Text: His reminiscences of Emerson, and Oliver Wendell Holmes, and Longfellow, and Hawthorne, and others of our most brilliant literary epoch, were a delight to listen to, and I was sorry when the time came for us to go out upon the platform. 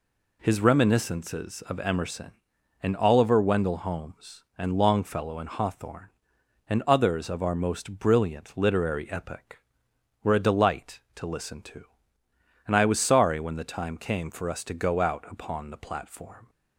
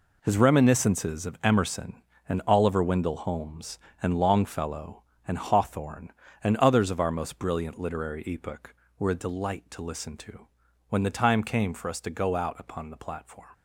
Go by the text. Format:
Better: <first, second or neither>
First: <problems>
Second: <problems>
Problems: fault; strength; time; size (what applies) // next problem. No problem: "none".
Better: first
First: none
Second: skips "and I was sorry"; at 10.6 s